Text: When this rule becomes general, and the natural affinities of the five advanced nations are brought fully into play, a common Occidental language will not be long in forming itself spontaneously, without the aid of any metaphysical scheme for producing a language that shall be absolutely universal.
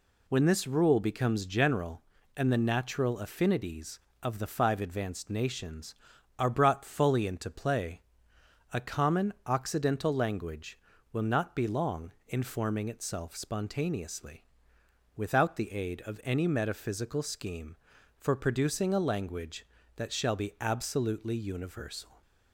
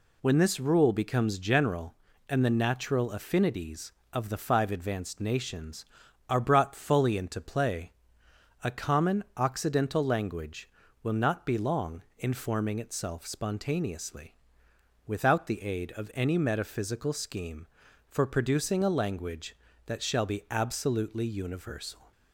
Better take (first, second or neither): neither